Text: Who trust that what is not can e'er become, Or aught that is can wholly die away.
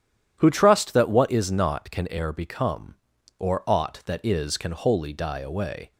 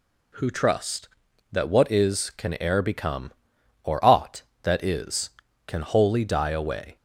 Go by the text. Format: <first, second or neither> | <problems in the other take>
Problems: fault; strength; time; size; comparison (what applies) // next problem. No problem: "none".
first | skips "not"; at 2.3 s